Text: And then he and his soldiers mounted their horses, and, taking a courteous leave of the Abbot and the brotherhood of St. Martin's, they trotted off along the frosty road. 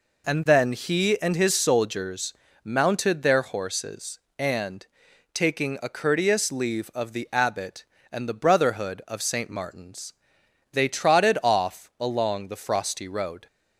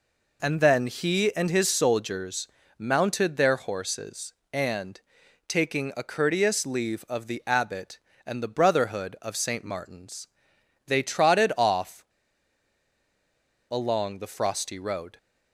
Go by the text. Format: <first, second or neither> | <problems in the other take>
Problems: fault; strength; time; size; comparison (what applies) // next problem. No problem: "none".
first | pauses between "soldiers" and "mounted"; slight; at 2.4 s; 0.32 s long; slight in the first // pauses between "off" and "along"; strong; at 12.0 s; 1.6 s long